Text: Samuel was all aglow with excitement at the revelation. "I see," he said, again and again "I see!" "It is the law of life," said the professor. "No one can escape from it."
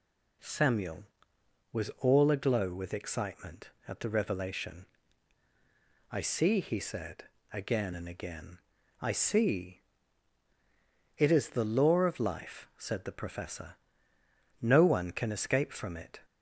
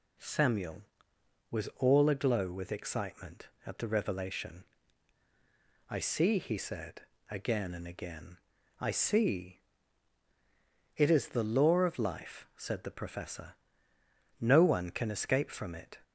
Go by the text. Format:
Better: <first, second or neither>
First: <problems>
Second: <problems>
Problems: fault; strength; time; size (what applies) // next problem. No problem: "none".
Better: neither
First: pauses between "again" and "I"; at 8.5 s; 0.42 s long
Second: pauses between "again" and "I"; at 8.3 s; 0.42 s long